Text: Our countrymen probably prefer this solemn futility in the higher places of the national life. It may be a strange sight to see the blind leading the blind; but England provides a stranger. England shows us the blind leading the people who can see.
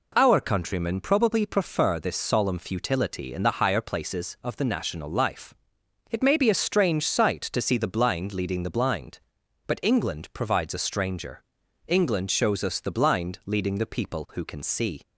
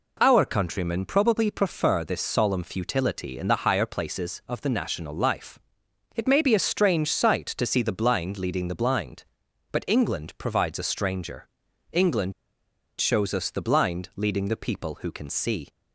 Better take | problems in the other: first | pauses between "England" and "shows"; noticeable; at 12.3 s; 0.66 s long

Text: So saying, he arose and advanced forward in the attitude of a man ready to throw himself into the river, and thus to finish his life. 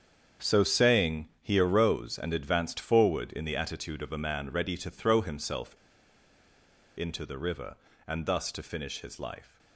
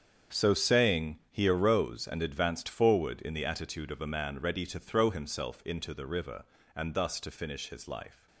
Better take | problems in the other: second | starts louder than the rest; strong; until 1.5 s; 7.5 dB; strong in the second // pauses between "himself" and "into"; at 5.7 s; 1.2 s long

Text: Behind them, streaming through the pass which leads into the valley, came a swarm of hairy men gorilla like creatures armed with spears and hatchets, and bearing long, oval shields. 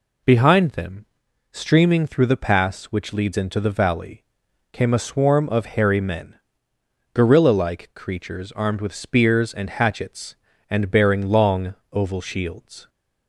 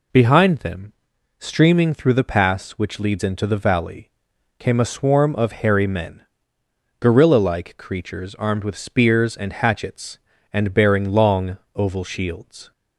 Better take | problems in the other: neither | pauses between "men" and "gorilla"; noticeable; the same in both

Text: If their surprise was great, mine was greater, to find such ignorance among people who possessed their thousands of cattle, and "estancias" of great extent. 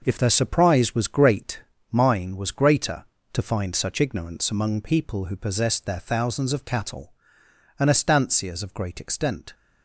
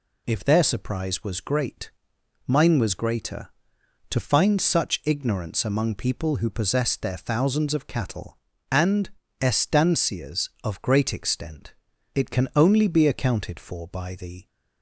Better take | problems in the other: first | pauses between "and" and "estancias"; slight; at 9.0 s; 0.32 s long // goes on to say "It can only be accounted for by the"; strong; from 12.1 s on; 2.3 s long

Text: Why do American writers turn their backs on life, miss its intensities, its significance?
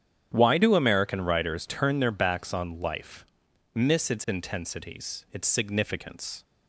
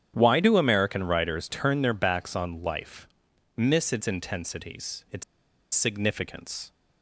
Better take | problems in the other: first | starts louder than the rest; strong; until 1.1 s; 9 dB; strong in the first // pauses between "its" and "significance"; noticeable; at 5.2 s; 0.51 s long

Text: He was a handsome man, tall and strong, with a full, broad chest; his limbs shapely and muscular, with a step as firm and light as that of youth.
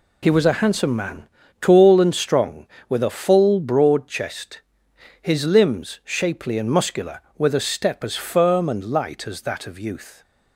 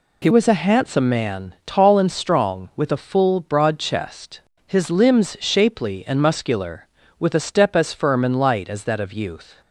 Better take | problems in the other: first | changes voice at "was"; from 0.3 s on; 9.3 s long

